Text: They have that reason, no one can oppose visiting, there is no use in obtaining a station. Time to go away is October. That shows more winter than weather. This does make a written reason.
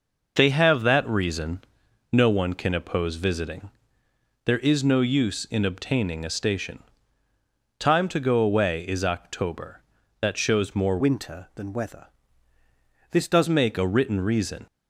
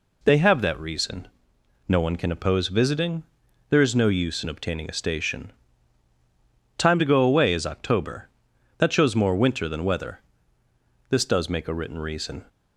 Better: second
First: changes voice from "winter" to "does"; from 11.0 to 13.4 s; 2.4 s long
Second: none

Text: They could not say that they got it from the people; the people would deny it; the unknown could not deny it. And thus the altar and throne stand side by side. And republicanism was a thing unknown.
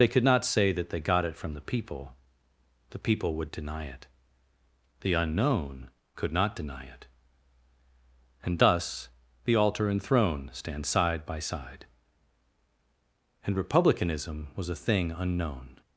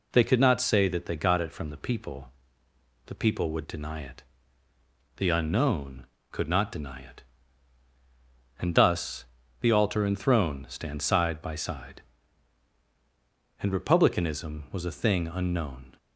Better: second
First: loses the start of "They"; at 0.0 s; 35 ms // pauses between "thus" and "the"; slight; at 9.0 s; 0.36 s long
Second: pauses between "thus" and "the"; slight; at 9.2 s; 0.36 s long

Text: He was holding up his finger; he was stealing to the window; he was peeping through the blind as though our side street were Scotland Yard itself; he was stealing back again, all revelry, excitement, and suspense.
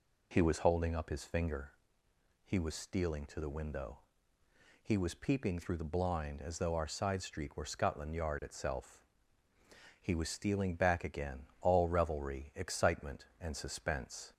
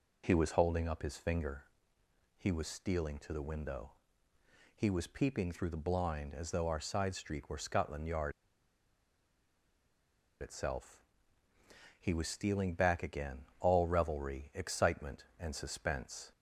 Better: first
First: none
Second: pauses between "Yard" and "itself"; strong; at 8.3 s; 2.0 s long

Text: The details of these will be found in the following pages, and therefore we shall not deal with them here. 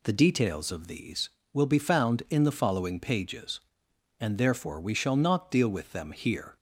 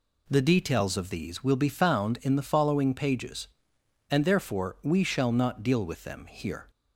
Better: neither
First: none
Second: none

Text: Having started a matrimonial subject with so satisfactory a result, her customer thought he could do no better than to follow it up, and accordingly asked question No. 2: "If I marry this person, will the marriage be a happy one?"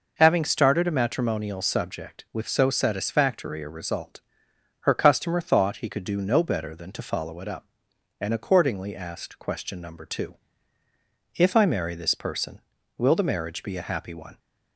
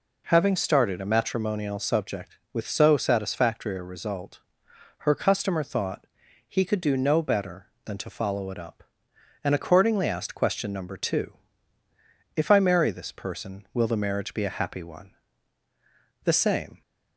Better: first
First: none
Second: pauses between "thought" and "he"; at 6.0 s; 0.40 s long // goes on to say "The same"; from 16.2 s on; 0.58 s long

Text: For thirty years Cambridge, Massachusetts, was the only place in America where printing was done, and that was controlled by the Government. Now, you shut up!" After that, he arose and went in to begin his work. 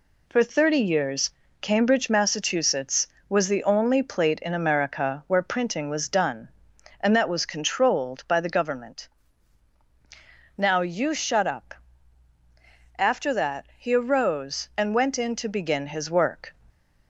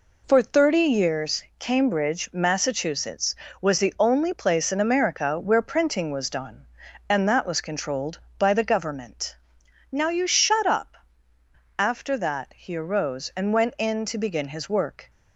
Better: second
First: pauses between "years" and "Cambridge"; slight; at 1.3 s; 0.30 s long // says "plate" for "place"; at 4.0 s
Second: none

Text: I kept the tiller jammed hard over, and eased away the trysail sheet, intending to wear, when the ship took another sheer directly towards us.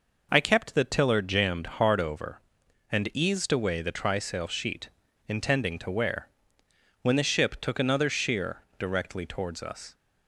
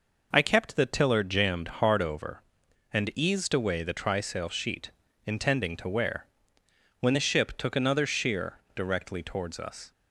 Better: neither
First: pauses between "sheer" and "directly"; slight; at 8.6 s; 0.16 s long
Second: pauses between "sheer" and "directly"; slight; at 8.5 s; 0.16 s long

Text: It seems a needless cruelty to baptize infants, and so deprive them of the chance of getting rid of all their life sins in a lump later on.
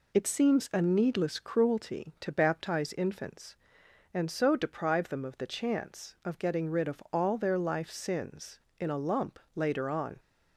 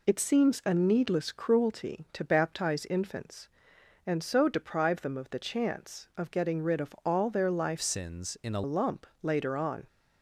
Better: first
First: pauses between "lump" and "later"; slight; at 9.3 s; 0.16 s long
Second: changes voice from "sins" to "a"; from 7.7 to 8.6 s; 0.9 s long // pauses between "lump" and "later"; slight; at 9.0 s; 0.16 s long

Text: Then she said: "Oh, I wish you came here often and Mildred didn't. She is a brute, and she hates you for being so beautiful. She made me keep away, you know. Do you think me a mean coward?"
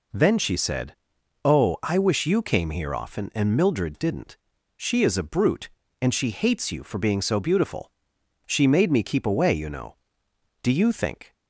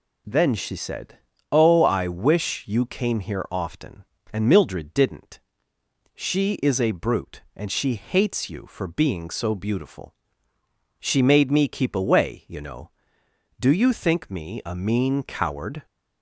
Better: second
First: stops before "me a mean coward"; at 11.3 s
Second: none

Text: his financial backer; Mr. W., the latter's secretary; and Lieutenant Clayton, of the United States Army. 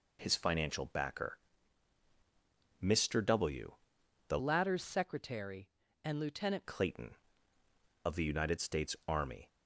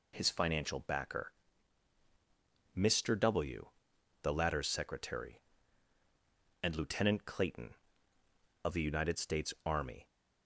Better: second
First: changes voice from "latter's" to "Lieutenant"; from 4.3 to 6.6 s; 2.3 s long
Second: none

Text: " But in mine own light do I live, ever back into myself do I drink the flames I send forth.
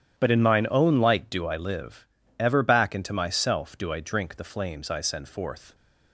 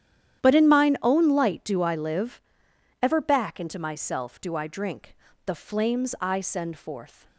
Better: first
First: starts louder than the rest; strong; until 1.2 s; 10.5 dB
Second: starts louder than the rest; strong; until 1.4 s; 10.5 dB // changes voice at "But"; from 0.4 s on; 6.8 s long // pauses between "drink" and "the"; slight; at 5.1 s; 0.32 s long

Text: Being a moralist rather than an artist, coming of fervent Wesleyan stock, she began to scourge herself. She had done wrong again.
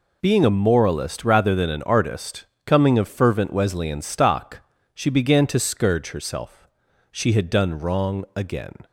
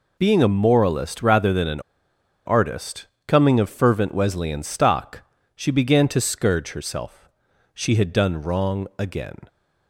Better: first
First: none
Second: pauses between "an" and "artist"; noticeable; at 1.7 s; 0.66 s long

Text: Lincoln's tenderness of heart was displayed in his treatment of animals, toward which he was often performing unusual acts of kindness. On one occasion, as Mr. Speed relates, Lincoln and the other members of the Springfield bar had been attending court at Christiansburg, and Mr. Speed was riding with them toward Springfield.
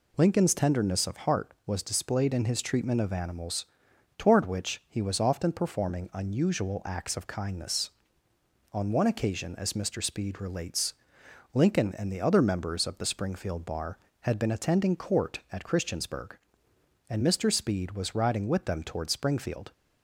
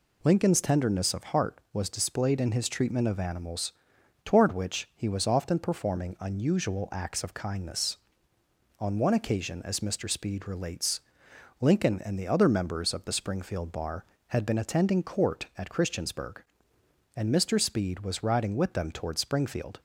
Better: neither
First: none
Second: none

